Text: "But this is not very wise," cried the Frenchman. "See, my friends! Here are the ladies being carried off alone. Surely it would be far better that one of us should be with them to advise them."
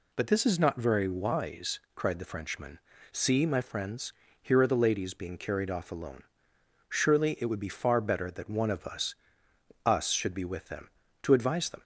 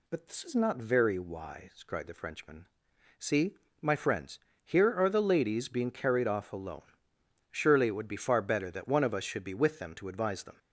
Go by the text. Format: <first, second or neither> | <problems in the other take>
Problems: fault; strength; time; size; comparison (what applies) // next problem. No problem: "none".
second | says "us" twice; at 9.8 s